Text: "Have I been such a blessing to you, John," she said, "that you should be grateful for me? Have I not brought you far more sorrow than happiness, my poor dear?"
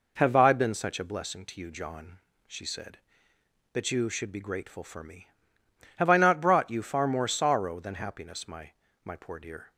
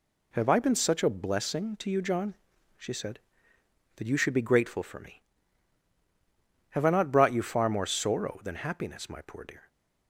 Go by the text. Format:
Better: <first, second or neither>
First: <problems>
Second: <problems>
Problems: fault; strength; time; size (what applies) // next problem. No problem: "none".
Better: second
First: says "my" twice; at 9.0 s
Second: none